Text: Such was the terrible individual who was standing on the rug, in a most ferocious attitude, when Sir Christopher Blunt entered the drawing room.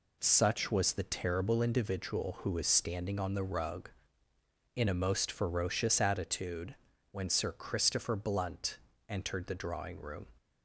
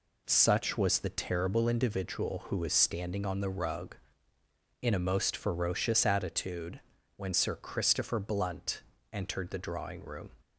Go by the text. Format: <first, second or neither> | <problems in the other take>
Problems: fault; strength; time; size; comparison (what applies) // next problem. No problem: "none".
neither | pauses between "Blunt" and "entered"; slight; the same in both